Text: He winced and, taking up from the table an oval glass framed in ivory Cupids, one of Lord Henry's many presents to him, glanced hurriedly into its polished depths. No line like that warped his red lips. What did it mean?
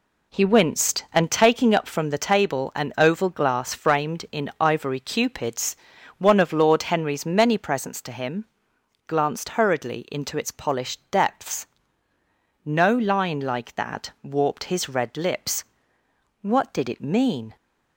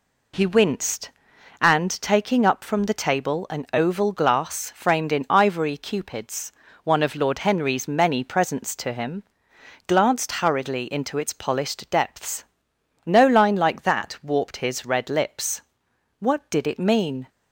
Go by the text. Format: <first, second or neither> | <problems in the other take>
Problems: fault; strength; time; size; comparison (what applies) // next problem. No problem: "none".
neither | none